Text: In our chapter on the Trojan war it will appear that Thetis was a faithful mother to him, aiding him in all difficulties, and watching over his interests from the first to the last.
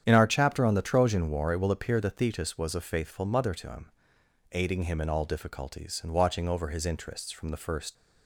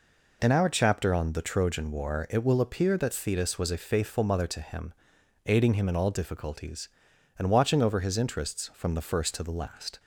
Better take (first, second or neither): second